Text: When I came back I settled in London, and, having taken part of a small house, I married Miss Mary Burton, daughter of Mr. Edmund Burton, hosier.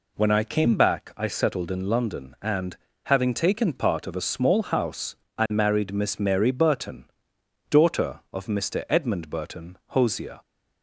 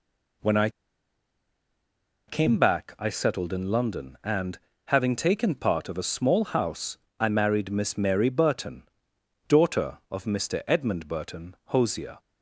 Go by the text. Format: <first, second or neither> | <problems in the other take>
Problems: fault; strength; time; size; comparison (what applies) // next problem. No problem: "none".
first | pauses between "I" and "came"; strong; at 0.6 s; 1.5 s long